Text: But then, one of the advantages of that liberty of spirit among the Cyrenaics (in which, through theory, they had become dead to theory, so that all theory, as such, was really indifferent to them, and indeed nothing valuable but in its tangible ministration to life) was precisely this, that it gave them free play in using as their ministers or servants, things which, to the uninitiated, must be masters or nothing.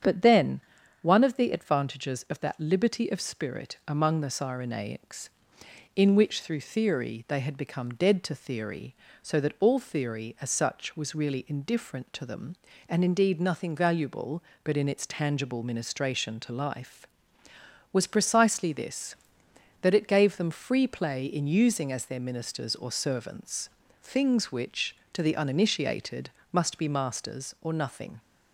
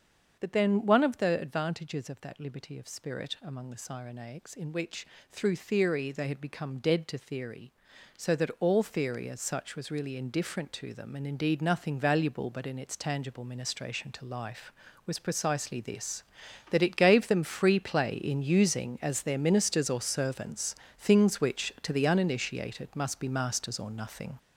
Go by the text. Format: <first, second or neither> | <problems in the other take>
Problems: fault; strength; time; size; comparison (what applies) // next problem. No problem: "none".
first | gets louder; throughout; 7 dB // starts louder than the rest; until 1.4 s; 7 dB; strong in the first